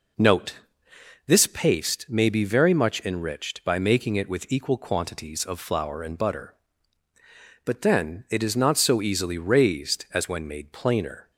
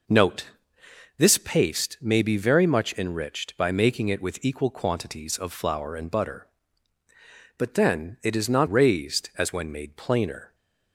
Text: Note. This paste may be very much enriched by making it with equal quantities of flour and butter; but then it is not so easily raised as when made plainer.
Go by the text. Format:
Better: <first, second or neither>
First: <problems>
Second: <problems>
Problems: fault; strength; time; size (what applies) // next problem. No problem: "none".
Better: first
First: none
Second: skips "so easily"; at 8.6 s